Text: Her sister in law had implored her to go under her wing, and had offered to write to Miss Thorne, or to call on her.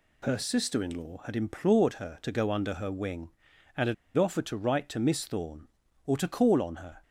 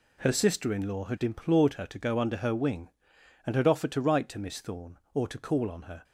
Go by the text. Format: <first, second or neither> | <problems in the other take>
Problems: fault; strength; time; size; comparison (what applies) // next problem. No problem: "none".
second | pauses between "had" and "offered"; slight; at 3.9 s; 0.22 s long